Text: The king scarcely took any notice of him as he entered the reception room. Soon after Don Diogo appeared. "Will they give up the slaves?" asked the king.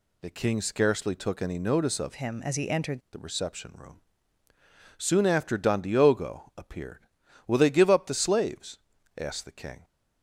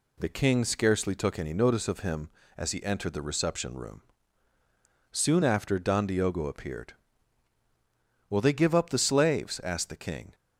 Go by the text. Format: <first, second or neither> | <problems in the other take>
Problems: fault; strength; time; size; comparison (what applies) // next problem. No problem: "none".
second | changes voice from "him" to "entered"; from 2.1 to 3.0 s; 0.9 s long